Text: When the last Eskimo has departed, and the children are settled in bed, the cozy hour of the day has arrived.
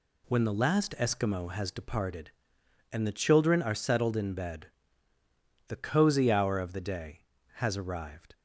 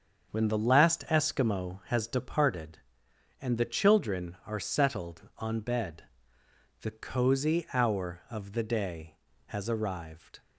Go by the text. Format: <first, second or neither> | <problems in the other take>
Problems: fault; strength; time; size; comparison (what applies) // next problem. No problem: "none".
first | starts louder than the rest; until 1.3 s; 7 dB // says "on" for "in"; at 5.3 s